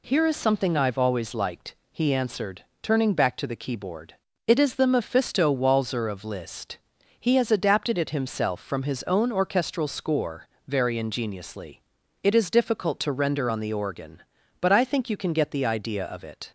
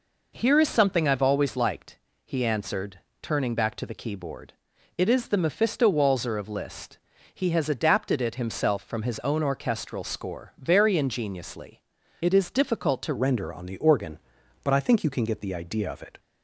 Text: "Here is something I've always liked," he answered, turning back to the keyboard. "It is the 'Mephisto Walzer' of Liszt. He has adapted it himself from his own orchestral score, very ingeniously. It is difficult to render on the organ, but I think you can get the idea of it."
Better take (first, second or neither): first